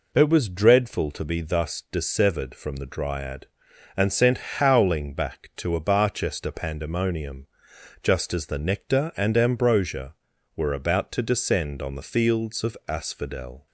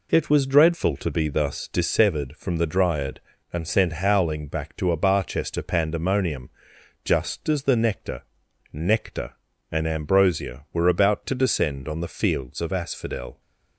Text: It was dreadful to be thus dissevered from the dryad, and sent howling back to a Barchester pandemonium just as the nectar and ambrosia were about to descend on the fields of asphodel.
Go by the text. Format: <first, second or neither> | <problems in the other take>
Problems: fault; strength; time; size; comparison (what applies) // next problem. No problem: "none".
first | pauses between "pandemonium" and "just"; noticeable; at 6.5 s; 0.52 s long; noticeable in the first // says "nectar" twice; at 8.7 s